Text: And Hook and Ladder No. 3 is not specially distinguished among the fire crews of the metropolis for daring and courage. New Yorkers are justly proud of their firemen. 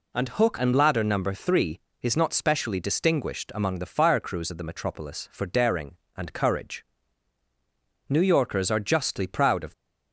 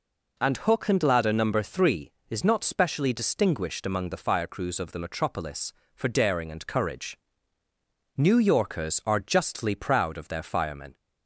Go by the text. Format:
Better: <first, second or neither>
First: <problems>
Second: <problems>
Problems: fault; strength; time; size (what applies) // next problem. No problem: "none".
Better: second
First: stops before "their firemen"; at 9.7 s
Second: none